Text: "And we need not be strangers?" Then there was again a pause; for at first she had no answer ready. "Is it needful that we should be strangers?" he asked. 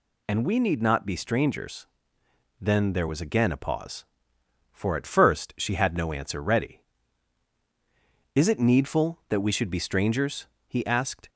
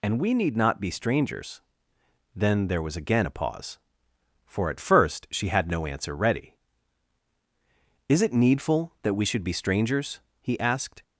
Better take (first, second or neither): neither